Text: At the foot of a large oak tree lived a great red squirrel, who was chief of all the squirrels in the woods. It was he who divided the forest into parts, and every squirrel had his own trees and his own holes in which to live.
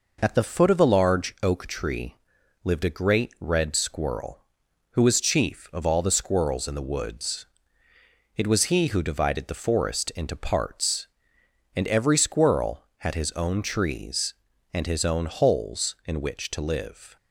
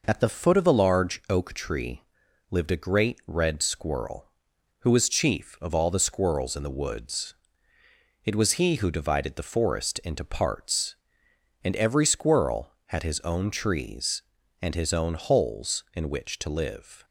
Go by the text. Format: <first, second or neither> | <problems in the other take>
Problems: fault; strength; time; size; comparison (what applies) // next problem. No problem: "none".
neither | pauses between "tree" and "lived"; noticeable; the same in both